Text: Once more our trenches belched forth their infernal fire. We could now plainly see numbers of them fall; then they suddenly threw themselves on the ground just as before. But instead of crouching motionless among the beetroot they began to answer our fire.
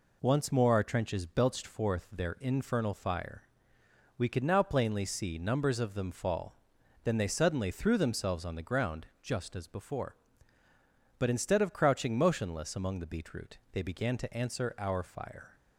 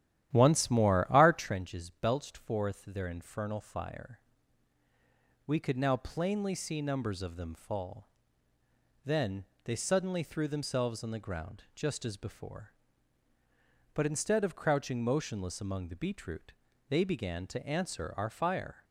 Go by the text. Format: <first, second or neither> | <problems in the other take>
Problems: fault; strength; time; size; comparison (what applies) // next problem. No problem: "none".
first | starts louder than the rest; strong; until 1.6 s; 11.5 dB // pauses between "then" and "they"; slight; at 9.4 s; 0.22 s long // pauses between "beetroot" and "they"; slight; at 16.5 s; 0.36 s long